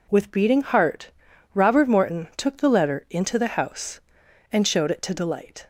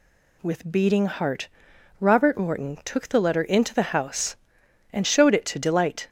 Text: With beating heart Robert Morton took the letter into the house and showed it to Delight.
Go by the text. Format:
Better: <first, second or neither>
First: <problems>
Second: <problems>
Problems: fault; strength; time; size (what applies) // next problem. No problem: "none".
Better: neither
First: pauses between "heart" and "Robert"; at 1.1 s; 0.42 s long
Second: pauses between "heart" and "Robert"; noticeable; at 1.4 s; 0.50 s long